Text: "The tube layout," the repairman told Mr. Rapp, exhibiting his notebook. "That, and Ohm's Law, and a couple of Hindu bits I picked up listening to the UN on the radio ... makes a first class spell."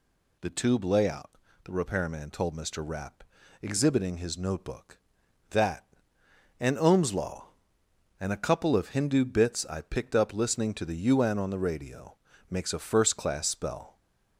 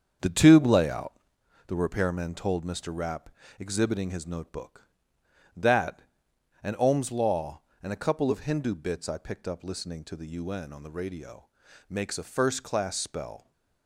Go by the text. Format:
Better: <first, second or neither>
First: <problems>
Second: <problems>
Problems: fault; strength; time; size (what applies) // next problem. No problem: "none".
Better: first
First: none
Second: starts louder than the rest; strong; until 1.5 s; 7.5 dB